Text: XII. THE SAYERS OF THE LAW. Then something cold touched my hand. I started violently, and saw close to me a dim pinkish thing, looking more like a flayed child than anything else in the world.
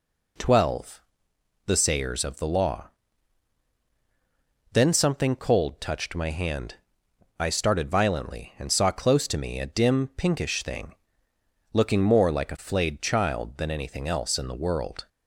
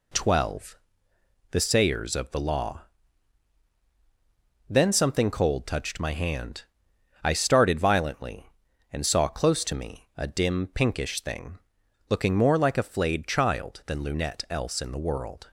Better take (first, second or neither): first